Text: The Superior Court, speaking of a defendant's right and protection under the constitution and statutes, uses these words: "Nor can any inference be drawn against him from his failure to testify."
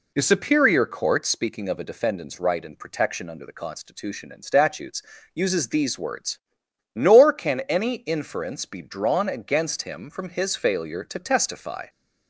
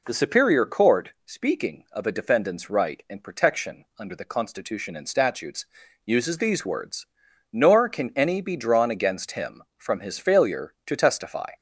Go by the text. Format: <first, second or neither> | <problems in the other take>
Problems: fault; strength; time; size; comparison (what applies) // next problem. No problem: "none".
first | skips "inference"; at 8.4 s